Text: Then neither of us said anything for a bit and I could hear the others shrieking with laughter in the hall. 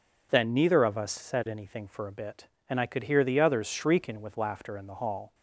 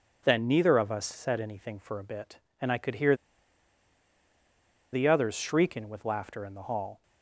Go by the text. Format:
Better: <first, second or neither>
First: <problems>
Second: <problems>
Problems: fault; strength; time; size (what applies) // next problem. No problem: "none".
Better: first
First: none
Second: pauses between "hear" and "the"; strong; at 3.1 s; 1.7 s long